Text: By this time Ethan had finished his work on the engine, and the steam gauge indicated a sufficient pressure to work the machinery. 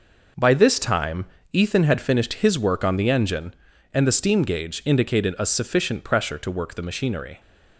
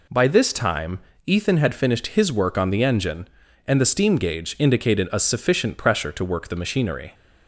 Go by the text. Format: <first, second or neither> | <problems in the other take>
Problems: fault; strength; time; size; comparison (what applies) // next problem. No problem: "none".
second | gets quieter; strong; throughout; 7.5 dB // pauses between "time" and "Ethan"; slight; at 1.2 s; 0.26 s long; slight in the second